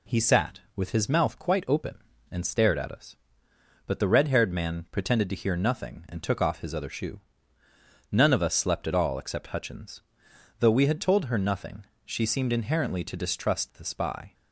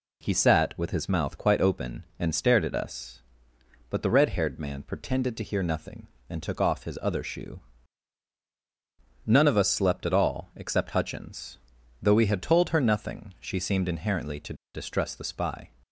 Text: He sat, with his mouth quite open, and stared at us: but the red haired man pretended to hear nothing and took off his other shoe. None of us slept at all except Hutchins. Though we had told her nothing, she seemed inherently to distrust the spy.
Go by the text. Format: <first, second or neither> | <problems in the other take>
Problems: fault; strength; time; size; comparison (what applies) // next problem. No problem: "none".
first | pauses between "to" and "distrust"; slight; at 14.5 s; 0.20 s long